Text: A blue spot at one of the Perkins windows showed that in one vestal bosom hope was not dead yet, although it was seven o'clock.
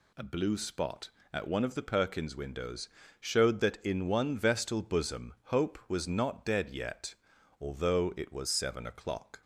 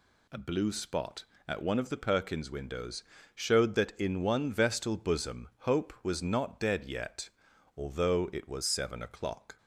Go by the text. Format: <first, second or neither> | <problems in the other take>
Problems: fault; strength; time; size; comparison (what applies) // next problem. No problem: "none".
neither | pauses between "windows" and "showed"; slight; the same in both